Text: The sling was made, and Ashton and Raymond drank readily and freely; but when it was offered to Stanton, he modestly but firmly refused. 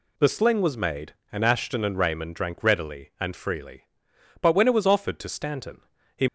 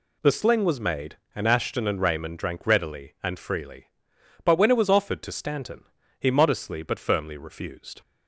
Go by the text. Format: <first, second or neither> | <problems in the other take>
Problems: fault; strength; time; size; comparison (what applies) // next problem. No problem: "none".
second | stops before "modestly but firmly refused"; at 6.2 s